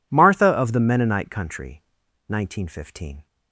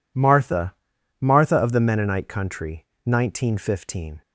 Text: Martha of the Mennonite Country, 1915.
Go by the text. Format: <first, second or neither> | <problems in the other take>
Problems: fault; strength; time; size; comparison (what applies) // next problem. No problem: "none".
first | says "Martha" twice; at 1.2 s